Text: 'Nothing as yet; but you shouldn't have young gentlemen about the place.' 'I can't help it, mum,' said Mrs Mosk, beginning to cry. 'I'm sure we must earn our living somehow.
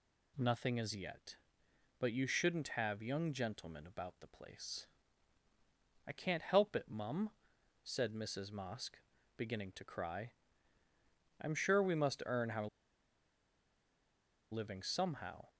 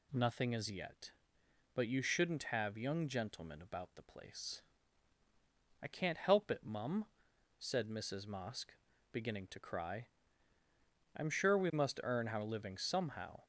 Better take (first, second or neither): second